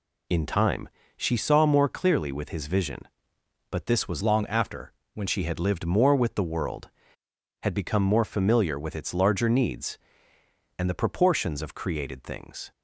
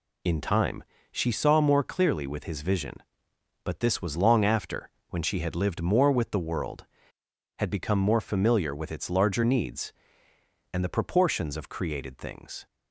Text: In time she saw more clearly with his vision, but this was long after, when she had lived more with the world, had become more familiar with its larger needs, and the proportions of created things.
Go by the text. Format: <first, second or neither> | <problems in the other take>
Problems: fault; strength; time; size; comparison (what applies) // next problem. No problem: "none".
second | pauses between "time" and "she"; slight; at 0.8 s; 0.28 s long; slight in the second // changes voice from "long" to "when"; from 4.2 to 5.2 s; 1.0 s long